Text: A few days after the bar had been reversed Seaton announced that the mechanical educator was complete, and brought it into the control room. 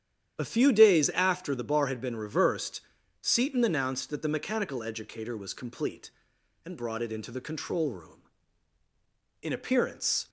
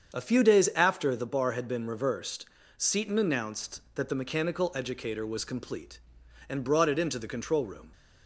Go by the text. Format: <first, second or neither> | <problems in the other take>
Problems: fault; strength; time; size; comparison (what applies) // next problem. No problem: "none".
second | starts louder than the rest; strong; until 1.4 s; 9.5 dB; strong in the second // pauses between "reversed" and "Seaton"; at 2.8 s; 0.42 s long; slight in the second // goes on to say "In appearance"; noticeable; from 9.4 s on; 0.86 s long